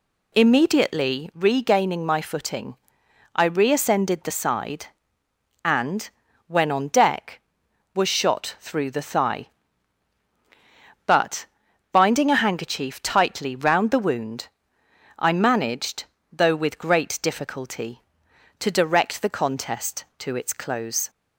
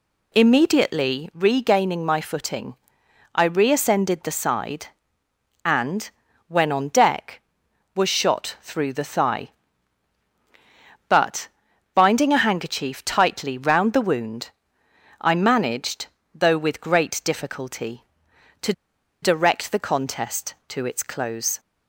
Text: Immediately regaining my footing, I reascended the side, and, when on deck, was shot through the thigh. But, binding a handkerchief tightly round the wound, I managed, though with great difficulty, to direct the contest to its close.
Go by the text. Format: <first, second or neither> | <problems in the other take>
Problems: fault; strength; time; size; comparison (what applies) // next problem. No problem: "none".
first | pauses between "to" and "direct"; noticeable; at 18.7 s; 0.50 s long